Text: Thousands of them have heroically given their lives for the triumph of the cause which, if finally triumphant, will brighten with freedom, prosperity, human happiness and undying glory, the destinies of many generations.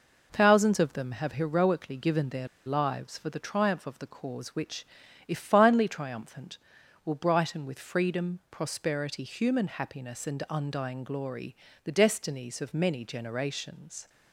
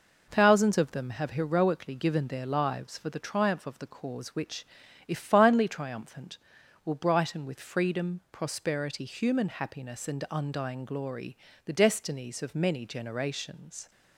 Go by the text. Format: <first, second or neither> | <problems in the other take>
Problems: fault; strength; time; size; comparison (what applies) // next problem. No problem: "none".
second | pauses between "their" and "lives"; slight; at 2.4 s; 0.19 s long